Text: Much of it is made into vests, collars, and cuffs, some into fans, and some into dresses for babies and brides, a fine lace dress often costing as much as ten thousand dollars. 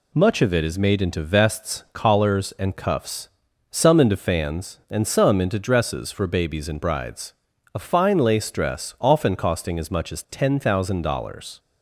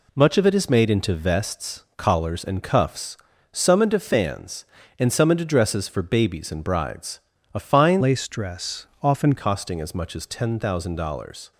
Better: first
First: none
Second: changes voice from "lace" to "often"; from 8.0 to 9.3 s; 1.3 s long // pauses between "dress" and "often"; slight; at 8.8 s; 0.16 s long

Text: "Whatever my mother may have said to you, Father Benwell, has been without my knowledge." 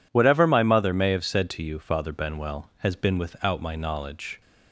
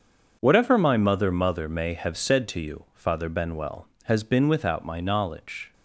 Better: first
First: none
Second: starts louder than the rest; until 1.4 s; 6.5 dB // says "mother" twice; at 1.3 s

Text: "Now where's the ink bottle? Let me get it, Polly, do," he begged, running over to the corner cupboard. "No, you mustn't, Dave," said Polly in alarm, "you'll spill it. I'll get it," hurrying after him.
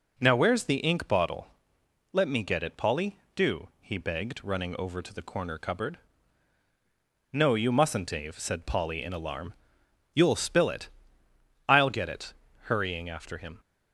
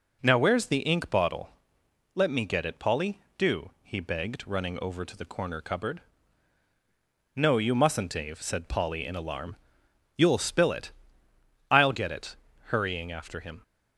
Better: neither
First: none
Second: none

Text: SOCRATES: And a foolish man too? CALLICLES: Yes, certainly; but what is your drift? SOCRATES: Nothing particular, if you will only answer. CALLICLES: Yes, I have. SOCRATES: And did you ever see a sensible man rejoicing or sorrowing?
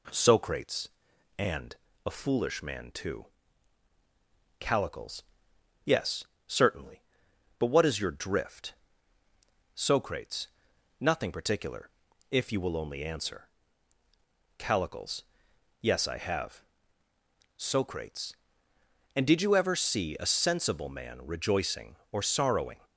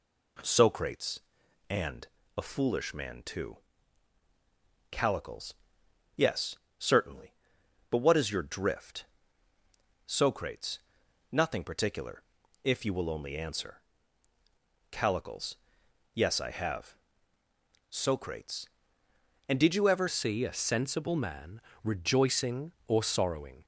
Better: first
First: pauses between "And" and "a"; slight; at 1.7 s; 0.30 s long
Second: pauses between "And" and "a"; slight; at 2.0 s; 0.30 s long // changes voice at "see"; from 20.0 s on; 3.6 s long // pauses between "man" and "rejoicing"; slight; at 21.6 s; 0.24 s long

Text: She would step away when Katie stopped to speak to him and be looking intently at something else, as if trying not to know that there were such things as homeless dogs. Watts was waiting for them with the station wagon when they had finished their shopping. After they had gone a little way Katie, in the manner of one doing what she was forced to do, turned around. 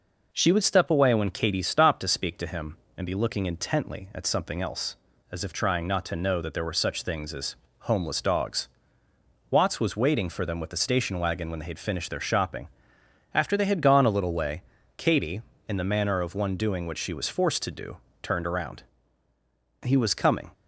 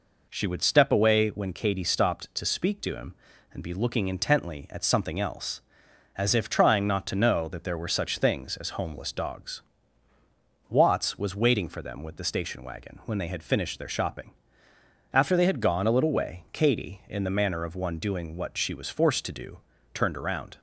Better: second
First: pauses between "as" and "homeless"; slight; at 7.5 s; 0.26 s long // pauses between "way" and "Katie"; slight; at 14.6 s; 0.34 s long // goes on to say "He was coming"; noticeable; from 19.8 s on; 0.70 s long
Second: none

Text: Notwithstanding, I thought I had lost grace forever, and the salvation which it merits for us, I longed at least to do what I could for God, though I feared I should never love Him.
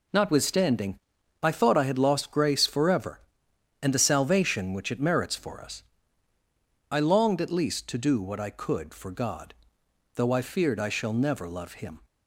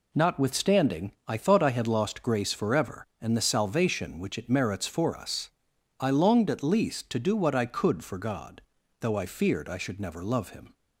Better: second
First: says "shall" for "should"; at 10.8 s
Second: none

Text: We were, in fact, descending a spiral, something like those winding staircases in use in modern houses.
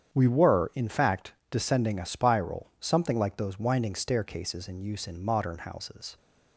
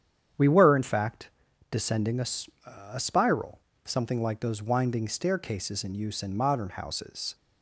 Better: first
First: starts louder than the rest; strong; until 1.1 s; 8.5 dB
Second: starts louder than the rest; strong; until 1.8 s; 9 dB // says "a" twice; at 2.9 s

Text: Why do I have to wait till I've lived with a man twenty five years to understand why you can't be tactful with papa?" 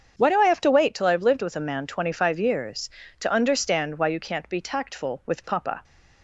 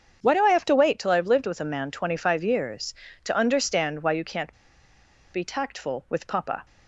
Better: first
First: starts louder than the rest; strong; until 1.1 s; 7.5 dB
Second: starts louder than the rest; strong; until 1.2 s; 7.5 dB // pauses between "can't" and "be"; noticeable; at 4.5 s; 0.80 s long

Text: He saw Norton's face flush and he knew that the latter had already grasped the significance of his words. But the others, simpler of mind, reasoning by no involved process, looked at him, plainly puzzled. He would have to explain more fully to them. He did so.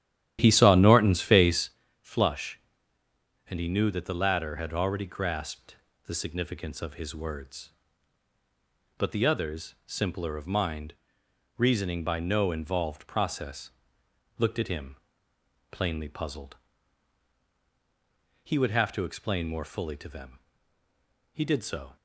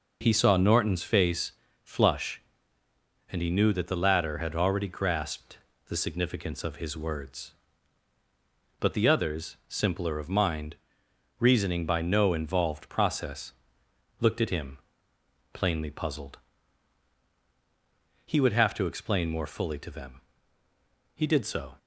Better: second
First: starts louder than the rest; strong; until 1.8 s; 11.5 dB // pauses between "face" and "flush"; slight; at 1.6 s; 0.32 s long // pauses between "grasped" and "the"; slight; at 5.7 s; 0.28 s long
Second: pauses between "face" and "flush"; slight; at 1.4 s; 0.32 s long // pauses between "grasped" and "the"; slight; at 5.5 s; 0.28 s long

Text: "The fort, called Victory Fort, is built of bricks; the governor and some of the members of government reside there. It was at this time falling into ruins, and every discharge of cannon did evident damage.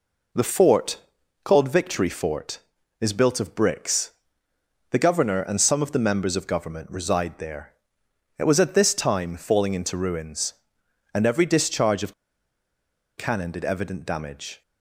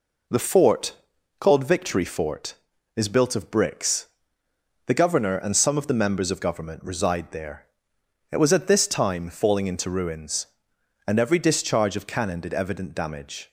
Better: second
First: pauses between "of" and "cannon"; at 12.1 s; 1.0 s long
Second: none

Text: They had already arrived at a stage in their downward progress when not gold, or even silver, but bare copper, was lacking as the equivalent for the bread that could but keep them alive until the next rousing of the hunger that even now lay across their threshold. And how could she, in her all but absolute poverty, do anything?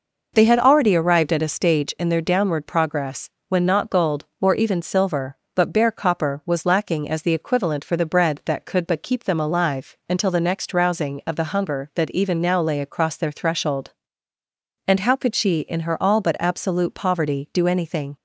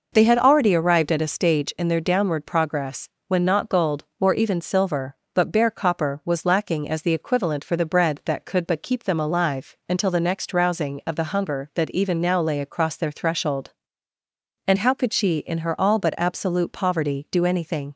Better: neither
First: pauses between "progress" and "when"; slight; at 3.3 s; 0.18 s long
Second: pauses between "progress" and "when"; slight; at 3.0 s; 0.18 s long

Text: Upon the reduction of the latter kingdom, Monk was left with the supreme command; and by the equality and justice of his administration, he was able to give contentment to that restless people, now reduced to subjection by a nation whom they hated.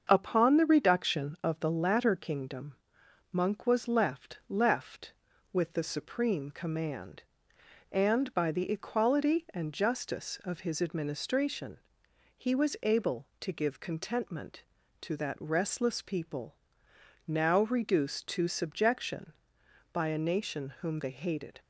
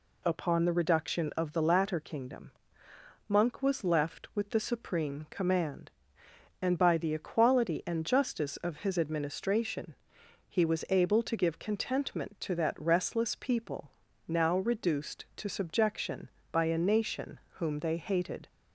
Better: second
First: starts louder than the rest; until 1.1 s; 7 dB // says "left" twice; at 4.4 s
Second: none

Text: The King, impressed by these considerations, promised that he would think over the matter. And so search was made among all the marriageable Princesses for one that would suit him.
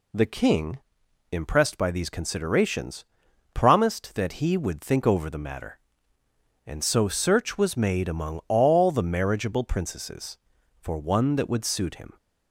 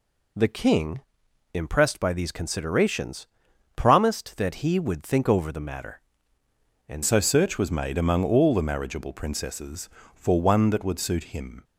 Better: first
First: none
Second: changes voice at "so"; from 7.0 s on; 4.6 s long

